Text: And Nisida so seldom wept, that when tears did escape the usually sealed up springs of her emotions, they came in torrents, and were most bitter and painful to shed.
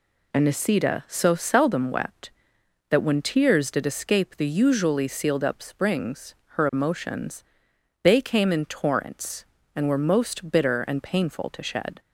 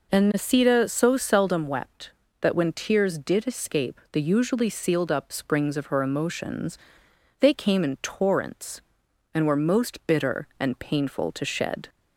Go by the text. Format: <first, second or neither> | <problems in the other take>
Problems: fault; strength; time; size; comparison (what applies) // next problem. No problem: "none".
second | skips "of"; at 6.4 s